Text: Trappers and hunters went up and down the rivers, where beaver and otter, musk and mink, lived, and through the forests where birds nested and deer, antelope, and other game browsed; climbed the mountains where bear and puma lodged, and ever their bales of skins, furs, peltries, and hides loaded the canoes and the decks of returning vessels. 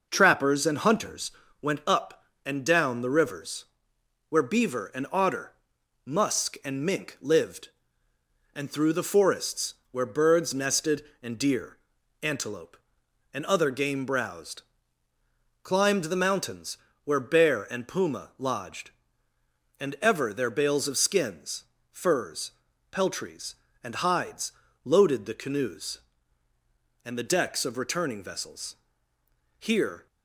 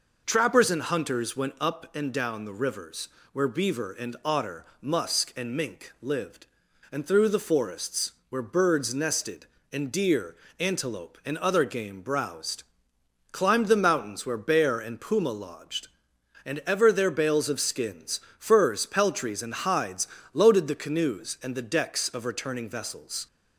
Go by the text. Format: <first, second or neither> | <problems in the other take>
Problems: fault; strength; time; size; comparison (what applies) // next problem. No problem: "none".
second | pauses between "hunters" and "went"; slight; at 1.3 s; 0.30 s long // pauses between "forests" and "where"; slight; at 9.7 s; 0.16 s long; slight in the second // pauses between "mountains" and "where"; slight; at 16.7 s; 0.28 s long // pauses between "hides" and "loaded"; slight; at 24.5 s; 0.32 s long; slight in the second // goes on to say "Here"; slight; from 29.6 s on; 0.46 s long